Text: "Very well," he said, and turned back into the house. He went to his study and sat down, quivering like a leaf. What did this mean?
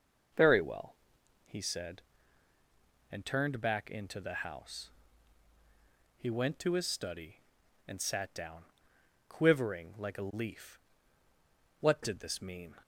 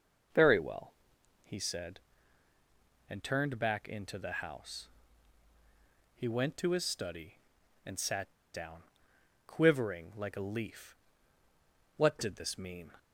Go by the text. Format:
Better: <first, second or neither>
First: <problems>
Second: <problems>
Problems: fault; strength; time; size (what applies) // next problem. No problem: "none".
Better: first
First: none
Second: pauses between "sat" and "down"; slight; at 8.3 s; 0.23 s long